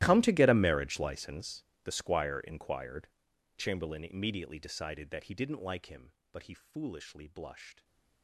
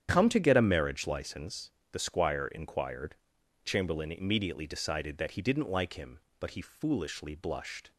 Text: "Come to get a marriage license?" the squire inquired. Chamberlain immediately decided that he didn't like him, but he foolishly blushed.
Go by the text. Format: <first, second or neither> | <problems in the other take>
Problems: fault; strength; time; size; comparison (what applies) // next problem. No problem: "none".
second | gets quieter; strong; throughout; 21.5 dB // starts louder than the rest; strong; until 1.0 s; 15 dB; strong in the second // stays silent after the last word; slight; from 7.7 s on; 0.5 s long